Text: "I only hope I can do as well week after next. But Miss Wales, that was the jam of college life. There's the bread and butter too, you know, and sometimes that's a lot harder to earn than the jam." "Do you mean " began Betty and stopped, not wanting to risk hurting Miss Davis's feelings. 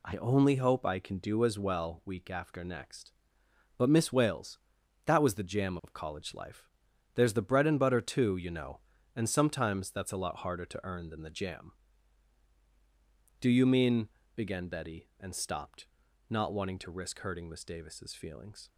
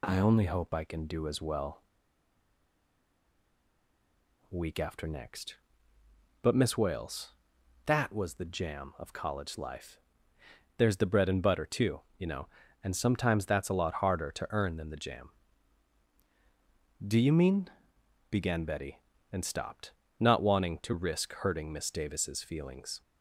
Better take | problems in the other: first | pauses between "well" and "week"; strong; at 1.8 s; 2.6 s long

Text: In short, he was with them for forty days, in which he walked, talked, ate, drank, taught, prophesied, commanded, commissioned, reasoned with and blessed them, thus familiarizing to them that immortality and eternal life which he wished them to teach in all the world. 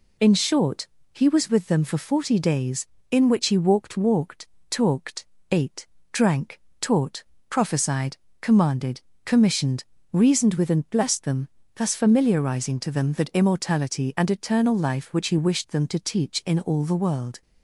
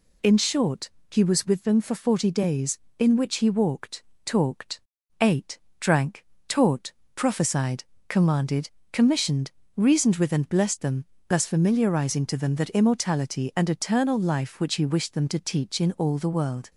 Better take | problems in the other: second | says "walked" twice; at 3.9 s

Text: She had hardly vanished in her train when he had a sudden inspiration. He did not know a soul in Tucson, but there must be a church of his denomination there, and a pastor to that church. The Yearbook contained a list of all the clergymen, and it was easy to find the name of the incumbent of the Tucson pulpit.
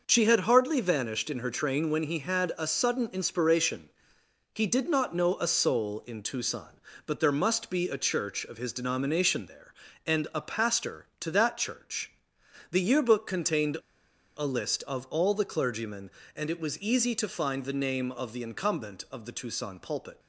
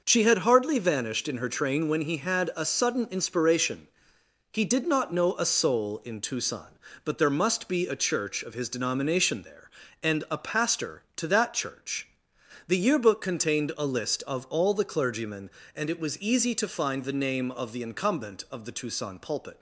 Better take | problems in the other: second | pauses between "contained" and "a"; noticeable; at 13.7 s; 0.58 s long

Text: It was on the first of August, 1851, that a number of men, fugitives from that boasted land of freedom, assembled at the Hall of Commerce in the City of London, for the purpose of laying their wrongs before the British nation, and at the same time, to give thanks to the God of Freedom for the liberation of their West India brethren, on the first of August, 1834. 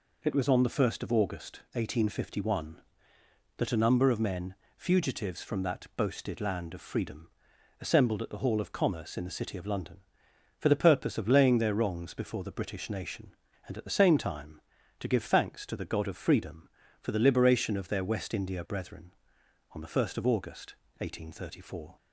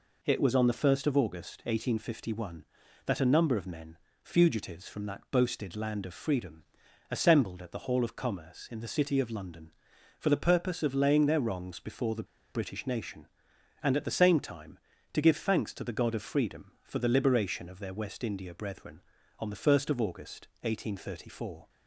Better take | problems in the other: first | pauses between "the" and "British"; slight; at 12.2 s; 0.29 s long

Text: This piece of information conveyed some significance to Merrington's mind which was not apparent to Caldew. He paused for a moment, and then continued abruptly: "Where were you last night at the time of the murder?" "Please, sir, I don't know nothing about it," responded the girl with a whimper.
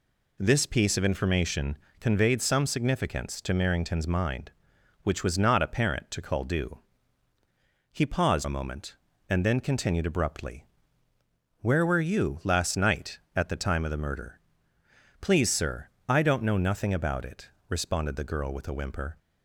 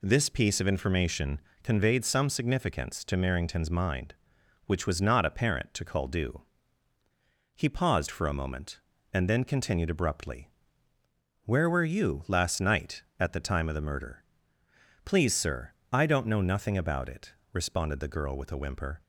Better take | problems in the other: second | pauses between "information" and "conveyed"; slight; at 1.7 s; 0.22 s long; slight in the second // skips "for"; at 8.4 s

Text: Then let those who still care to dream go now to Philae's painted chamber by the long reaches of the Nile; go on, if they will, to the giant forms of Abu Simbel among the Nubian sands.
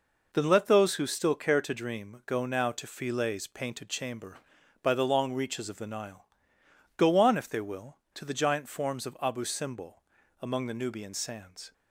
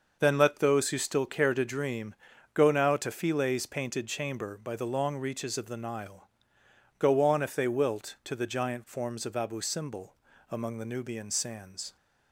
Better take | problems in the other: first | starts louder than the rest; noticeable; until 1.2 s; 6 dB // pauses between "dream" and "go"; at 2.1 s; 0.40 s long // says "wilt" for "will"; at 7.6 s // pauses between "Simbel" and "among"; slight; at 10.1 s; 0.34 s long; also in the first

